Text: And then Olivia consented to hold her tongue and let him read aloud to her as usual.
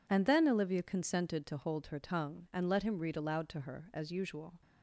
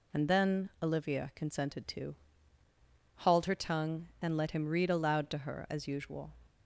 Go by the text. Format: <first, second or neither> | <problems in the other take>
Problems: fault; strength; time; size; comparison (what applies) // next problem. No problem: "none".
first | says "hauled" for "hold"; at 3.2 s